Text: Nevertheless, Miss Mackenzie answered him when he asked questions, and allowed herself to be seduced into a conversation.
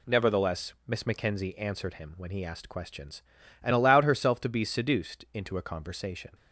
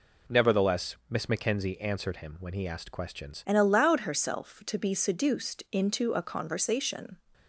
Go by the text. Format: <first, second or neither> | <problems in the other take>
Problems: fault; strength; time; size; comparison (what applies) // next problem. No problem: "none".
first | changes voice at "and"; from 3.4 s on; 3.7 s long